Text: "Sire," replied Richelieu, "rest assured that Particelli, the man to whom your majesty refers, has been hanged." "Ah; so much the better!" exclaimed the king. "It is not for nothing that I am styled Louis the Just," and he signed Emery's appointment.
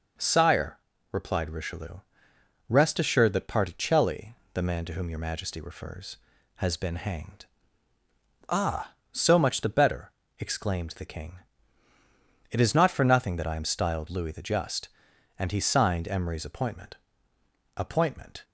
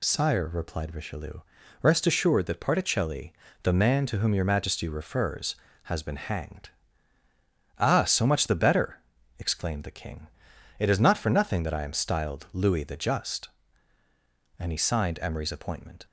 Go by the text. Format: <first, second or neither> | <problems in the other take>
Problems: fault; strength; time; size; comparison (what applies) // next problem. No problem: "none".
second | says "appointment" twice; at 17.7 s